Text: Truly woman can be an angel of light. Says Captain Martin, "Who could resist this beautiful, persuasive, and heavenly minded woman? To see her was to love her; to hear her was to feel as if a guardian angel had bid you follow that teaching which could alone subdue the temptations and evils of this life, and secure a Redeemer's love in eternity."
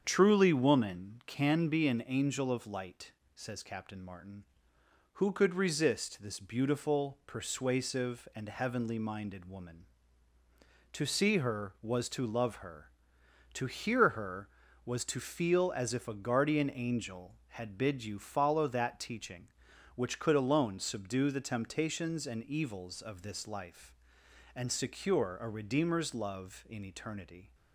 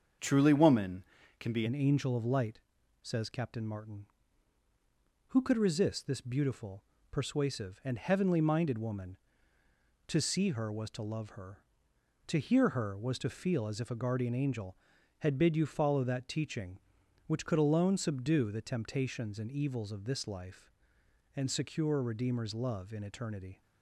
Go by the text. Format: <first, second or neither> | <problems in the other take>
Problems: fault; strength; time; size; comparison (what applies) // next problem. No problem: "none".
first | starts louder than the rest; until 1.5 s; 7 dB; strong in the first // changes voice at "an"; from 1.6 s on; 22.0 s long